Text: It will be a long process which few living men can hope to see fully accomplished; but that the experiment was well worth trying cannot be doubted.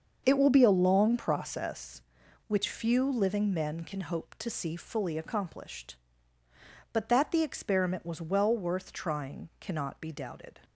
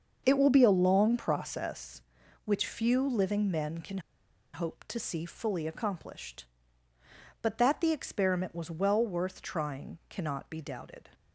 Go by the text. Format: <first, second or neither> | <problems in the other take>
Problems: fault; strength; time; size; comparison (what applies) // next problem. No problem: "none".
first | starts louder than the rest; until 1.2 s; 6.5 dB; also in the first // pauses between "can" and "hope"; noticeable; at 3.9 s; 0.55 s long